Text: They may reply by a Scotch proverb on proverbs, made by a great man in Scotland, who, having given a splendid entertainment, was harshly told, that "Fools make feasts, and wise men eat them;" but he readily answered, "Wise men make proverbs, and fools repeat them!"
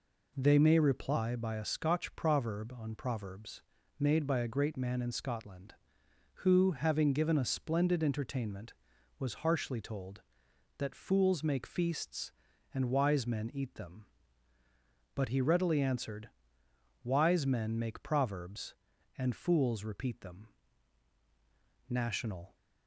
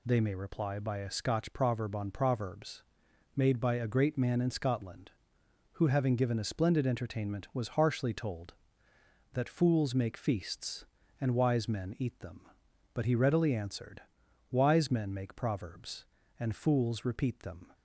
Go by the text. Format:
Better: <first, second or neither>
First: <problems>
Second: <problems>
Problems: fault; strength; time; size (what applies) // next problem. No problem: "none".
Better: second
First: goes on to say "National"; noticeable; from 21.9 s on; 0.64 s long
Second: none